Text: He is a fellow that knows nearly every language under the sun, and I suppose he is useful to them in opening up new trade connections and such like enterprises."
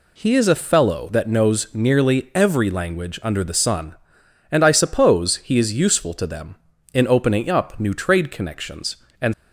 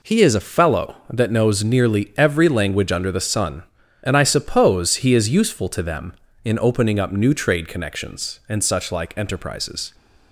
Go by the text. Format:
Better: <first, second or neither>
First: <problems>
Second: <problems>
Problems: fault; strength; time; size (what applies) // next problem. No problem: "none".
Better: second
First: stops before "such like enterprises"; at 9.3 s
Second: none